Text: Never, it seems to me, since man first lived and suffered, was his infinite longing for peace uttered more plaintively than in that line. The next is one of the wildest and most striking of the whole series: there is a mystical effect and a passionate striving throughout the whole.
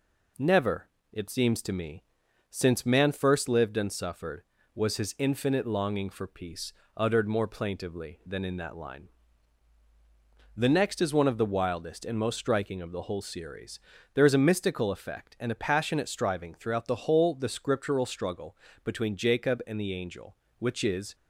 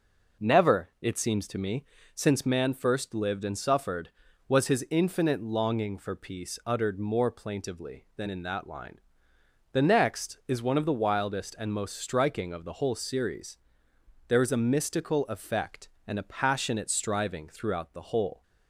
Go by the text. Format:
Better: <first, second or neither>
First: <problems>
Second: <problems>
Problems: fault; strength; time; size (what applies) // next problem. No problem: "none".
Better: second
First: pauses between "peace" and "uttered"; slight; at 6.7 s; 0.24 s long // goes on to say "The Scriptural struggle between Jacob and the angel which is"; strong; from 17.3 s on; 3.8 s long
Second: none